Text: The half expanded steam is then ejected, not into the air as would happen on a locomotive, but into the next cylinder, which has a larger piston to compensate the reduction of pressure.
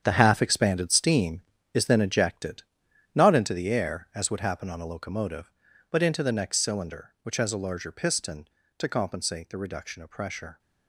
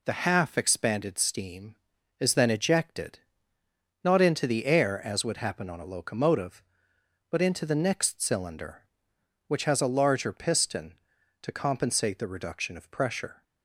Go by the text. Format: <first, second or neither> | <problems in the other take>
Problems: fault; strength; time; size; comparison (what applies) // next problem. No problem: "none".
second | gets quieter; strong; throughout; 11.5 dB